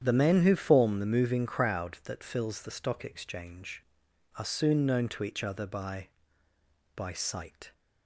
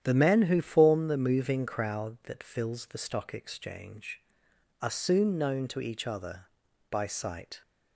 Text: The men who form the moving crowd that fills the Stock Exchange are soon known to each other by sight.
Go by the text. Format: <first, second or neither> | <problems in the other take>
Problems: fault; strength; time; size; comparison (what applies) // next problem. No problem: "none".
second | starts louder than the rest; strong; until 1.0 s; 9 dB; strong in the second // says "by" twice; at 6.9 s